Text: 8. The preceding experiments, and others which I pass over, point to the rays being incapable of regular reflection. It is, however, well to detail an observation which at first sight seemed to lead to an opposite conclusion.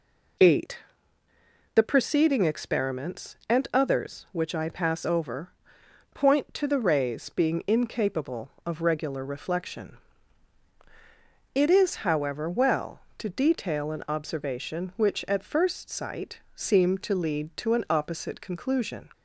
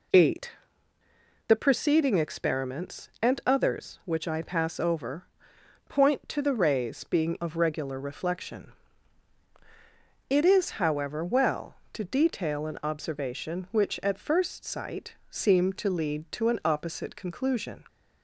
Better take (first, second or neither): first